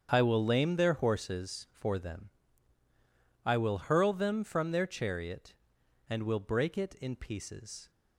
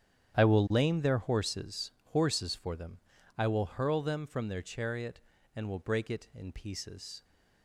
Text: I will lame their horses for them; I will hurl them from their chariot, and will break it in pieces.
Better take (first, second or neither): first